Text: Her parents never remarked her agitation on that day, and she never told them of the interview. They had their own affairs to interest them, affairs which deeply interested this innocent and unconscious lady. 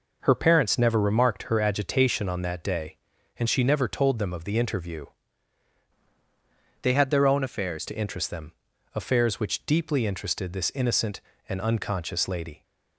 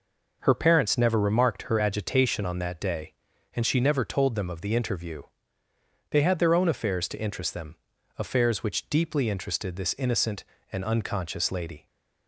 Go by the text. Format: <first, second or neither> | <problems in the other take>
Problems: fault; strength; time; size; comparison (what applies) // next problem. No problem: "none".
second | changes voice from "They" to "affairs"; from 6.8 to 7.8 s; 1.0 s long